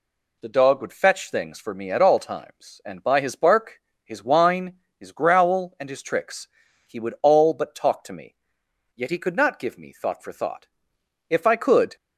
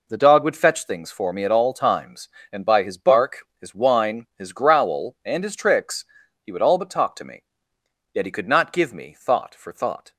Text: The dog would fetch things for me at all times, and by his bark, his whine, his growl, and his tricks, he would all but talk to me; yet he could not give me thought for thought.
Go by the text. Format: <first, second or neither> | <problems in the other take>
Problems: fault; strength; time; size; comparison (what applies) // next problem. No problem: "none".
second | goes on to say "If I could"; noticeable; from 11.2 s on; 0.68 s long